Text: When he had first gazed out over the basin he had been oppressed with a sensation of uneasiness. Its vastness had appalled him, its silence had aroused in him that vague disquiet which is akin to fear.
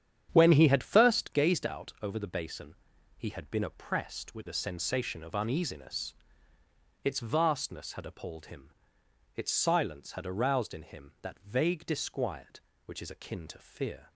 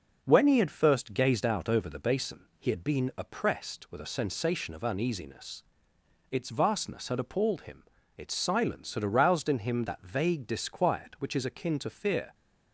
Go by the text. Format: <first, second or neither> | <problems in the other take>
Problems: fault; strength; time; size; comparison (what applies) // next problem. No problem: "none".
second | starts louder than the rest; strong; until 1.4 s; 9 dB // pauses between "basin" and "he"; at 2.7 s; 0.42 s long